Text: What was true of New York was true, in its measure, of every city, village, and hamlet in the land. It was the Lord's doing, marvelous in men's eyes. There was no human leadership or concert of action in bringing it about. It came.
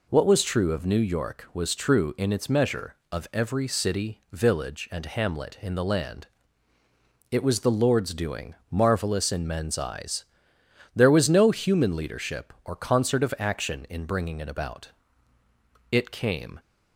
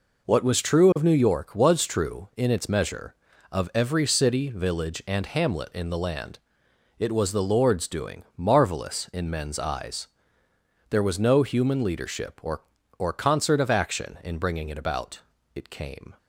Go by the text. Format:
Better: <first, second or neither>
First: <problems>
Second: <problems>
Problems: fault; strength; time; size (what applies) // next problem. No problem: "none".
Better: first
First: none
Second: says "or" twice; at 12.9 s